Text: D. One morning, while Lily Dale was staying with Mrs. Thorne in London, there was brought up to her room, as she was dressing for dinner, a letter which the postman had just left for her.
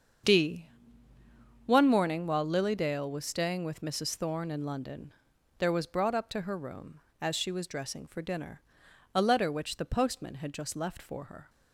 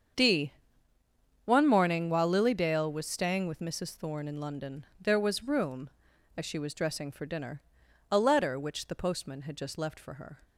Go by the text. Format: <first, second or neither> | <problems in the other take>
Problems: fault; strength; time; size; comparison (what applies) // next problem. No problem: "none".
first | starts louder than the rest; strong; until 2.0 s; 7.5 dB; also in the first // skips "brought up to her"; at 5.4 s